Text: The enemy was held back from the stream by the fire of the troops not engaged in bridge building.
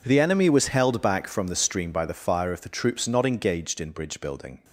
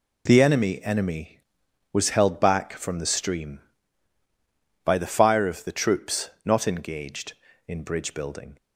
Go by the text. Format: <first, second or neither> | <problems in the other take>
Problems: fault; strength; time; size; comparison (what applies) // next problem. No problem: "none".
first | says "enemy" twice; at 0.8 s